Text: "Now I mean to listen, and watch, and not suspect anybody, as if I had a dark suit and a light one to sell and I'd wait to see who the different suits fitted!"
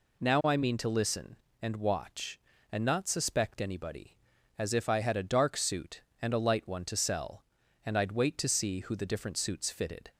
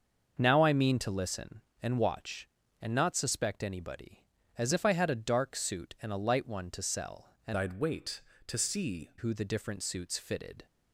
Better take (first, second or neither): first